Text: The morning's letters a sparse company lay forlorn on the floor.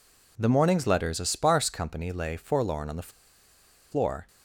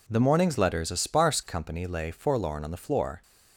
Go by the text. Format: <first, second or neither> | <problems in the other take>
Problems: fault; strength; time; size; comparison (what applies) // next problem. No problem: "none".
second | pauses between "the" and "floor"; noticeable; at 3.0 s; 0.82 s long